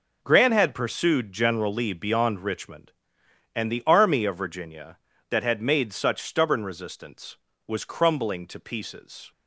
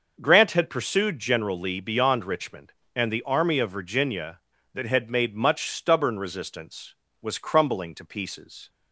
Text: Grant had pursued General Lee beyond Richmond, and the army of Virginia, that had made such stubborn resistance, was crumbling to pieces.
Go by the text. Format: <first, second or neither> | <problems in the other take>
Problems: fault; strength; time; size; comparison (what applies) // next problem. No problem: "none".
first | starts louder than the rest; noticeable; until 1.2 s; 6 dB // says "much" for "such"; at 5.3 s